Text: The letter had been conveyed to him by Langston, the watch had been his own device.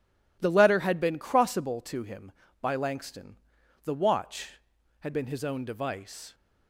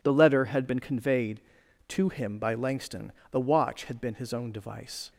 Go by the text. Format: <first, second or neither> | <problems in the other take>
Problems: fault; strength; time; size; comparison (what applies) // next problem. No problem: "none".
second | says "crossable" for "conveyed"; at 1.1 s